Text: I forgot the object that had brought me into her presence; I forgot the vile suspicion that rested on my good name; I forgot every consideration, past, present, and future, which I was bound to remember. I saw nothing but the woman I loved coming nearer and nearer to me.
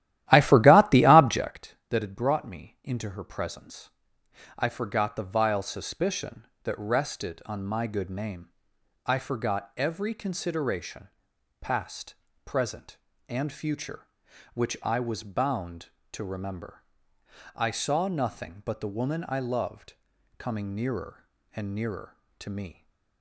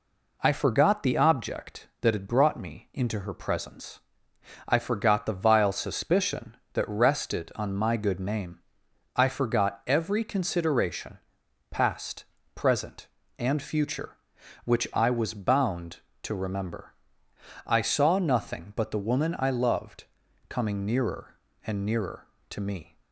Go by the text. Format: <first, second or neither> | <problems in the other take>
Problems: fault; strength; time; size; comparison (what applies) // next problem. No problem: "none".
second | starts louder than the rest; strong; until 1.6 s; 13.5 dB // pauses between "loved" and "coming"; noticeable; at 19.9 s; 0.46 s long; noticeable in the second